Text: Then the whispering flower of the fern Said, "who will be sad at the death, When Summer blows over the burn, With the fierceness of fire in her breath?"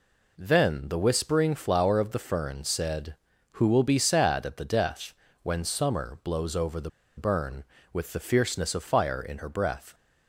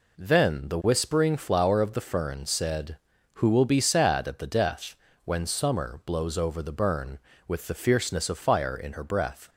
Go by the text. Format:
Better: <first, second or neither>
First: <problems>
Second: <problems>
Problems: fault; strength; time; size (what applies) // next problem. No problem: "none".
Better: second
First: pauses between "the" and "burn"; slight; at 6.8 s; 0.28 s long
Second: none